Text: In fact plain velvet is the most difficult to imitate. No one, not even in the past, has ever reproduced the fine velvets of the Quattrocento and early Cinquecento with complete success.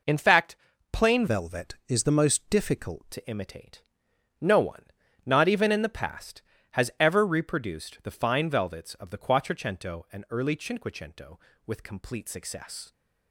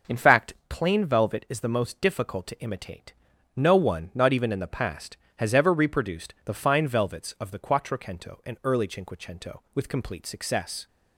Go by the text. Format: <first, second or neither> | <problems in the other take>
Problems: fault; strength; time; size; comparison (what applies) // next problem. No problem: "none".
second | pauses between "fact" and "plain"; slight; at 0.5 s; 0.36 s long; slight in the second // changes voice from "velvet" to "difficult"; from 1.2 to 3.1 s; 1.9 s long